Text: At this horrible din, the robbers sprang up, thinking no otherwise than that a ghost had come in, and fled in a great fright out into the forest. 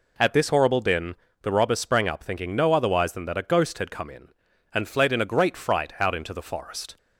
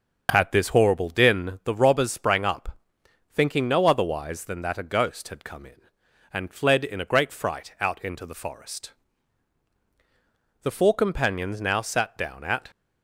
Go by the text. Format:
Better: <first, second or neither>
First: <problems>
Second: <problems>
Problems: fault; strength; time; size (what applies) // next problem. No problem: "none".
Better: first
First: none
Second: starts louder than the rest; until 1.3 s; 7 dB // goes on to say "The four companions now sat down at"; strong; from 10.6 s on; 2.0 s long